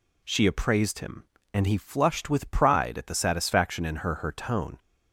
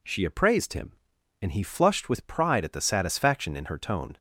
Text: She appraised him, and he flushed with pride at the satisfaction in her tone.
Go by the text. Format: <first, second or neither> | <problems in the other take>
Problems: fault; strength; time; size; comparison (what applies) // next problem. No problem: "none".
second | says "her" twice; at 4.1 s